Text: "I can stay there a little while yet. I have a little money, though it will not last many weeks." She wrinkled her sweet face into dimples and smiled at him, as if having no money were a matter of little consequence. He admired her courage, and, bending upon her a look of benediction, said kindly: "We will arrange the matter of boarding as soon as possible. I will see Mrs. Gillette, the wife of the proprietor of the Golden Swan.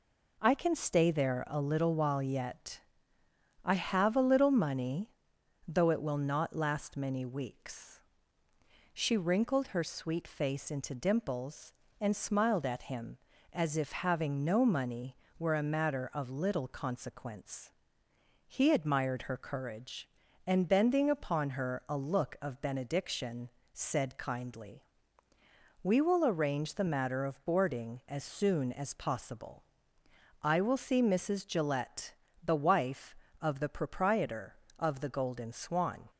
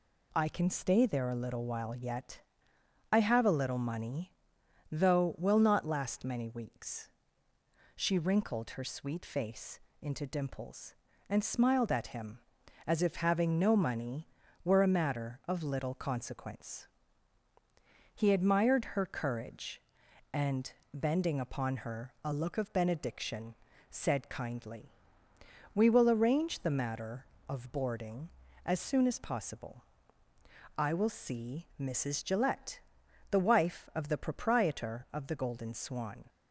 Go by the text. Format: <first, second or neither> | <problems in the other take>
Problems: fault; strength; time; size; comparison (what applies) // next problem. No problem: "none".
first | skips "it"; at 5.3 s // pauses between "face" and "into"; slight; at 9.7 s; 0.22 s long